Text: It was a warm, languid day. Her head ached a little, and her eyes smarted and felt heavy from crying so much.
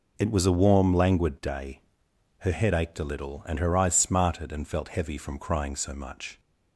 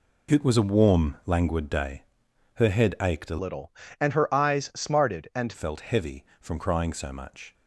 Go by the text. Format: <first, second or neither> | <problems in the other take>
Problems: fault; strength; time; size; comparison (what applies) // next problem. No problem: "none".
first | changes voice from "little" to "and"; from 3.3 to 5.5 s; 2.2 s long